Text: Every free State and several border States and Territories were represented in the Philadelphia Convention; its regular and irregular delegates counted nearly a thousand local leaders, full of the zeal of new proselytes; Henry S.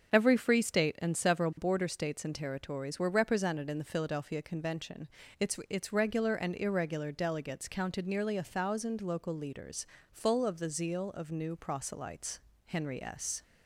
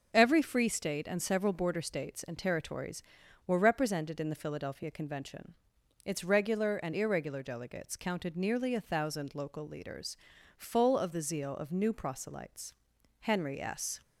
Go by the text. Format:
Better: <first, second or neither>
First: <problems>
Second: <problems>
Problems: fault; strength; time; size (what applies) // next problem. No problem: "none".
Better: second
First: starts louder than the rest; until 1.1 s; 7 dB // says "its" twice; at 5.6 s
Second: none